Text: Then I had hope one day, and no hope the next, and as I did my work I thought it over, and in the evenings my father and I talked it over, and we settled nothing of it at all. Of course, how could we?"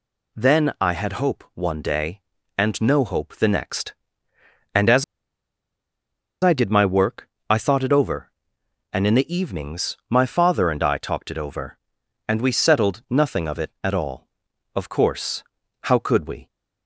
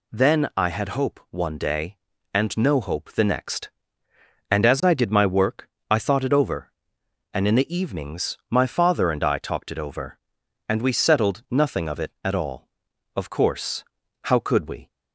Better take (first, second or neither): second